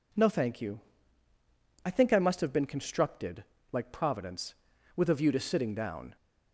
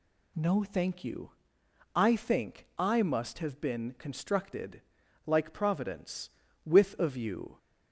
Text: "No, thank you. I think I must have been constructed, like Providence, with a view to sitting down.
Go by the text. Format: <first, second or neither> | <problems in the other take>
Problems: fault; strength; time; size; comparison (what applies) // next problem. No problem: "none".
first | stops before "to sitting down"; at 7.5 s